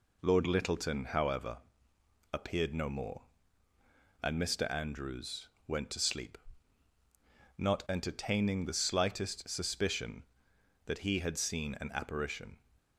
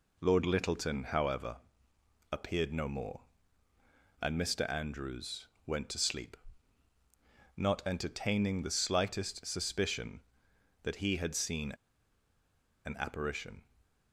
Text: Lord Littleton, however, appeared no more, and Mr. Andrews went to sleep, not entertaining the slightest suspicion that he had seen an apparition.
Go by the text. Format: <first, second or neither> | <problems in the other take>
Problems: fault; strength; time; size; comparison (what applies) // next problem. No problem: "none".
first | pauses between "Andrews" and "went"; slight; at 5.4 s; 0.22 s long; slight in the first // pauses between "seen" and "an"; at 11.7 s; 1.1 s long